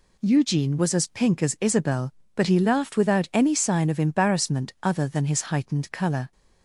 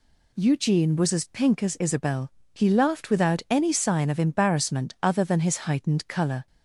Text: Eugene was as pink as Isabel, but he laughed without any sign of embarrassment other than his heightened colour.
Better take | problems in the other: first | skips "but"; at 2.4 s

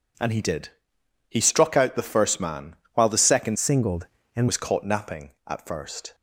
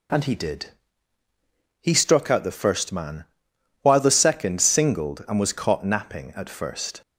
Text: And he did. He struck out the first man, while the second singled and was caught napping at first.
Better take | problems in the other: second | changes voice from "singled" to "and"; from 3.5 to 4.4 s; 0.9 s long

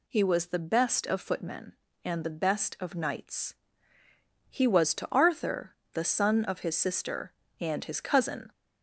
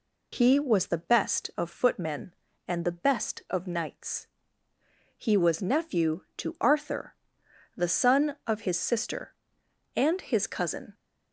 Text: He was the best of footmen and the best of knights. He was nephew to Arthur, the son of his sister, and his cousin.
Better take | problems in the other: second | skips "nephew"; at 4.9 s

